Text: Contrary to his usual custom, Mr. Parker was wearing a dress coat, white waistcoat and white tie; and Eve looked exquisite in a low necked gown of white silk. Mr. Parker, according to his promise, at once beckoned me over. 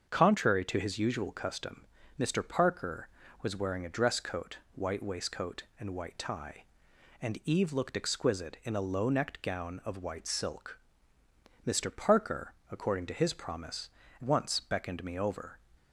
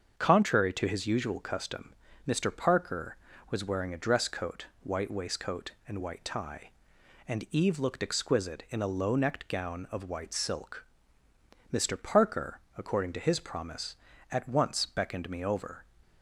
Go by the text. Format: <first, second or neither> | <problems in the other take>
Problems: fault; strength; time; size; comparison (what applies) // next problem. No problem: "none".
second | starts louder than the rest; until 1.1 s; 7 dB; also in the second // skips "at"; at 14.0 s